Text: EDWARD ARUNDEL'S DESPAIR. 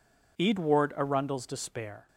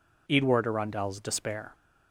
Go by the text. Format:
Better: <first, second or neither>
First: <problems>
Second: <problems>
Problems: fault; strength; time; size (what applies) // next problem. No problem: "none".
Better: neither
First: none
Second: none